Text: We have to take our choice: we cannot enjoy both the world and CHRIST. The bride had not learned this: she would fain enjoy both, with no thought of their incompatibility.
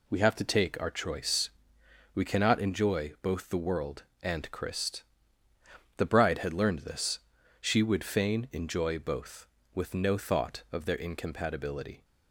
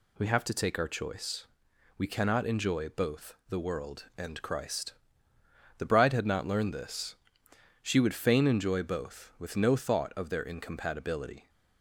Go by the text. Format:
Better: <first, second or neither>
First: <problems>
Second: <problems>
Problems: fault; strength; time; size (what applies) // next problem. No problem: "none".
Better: second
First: skips "not"; at 6.5 s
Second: none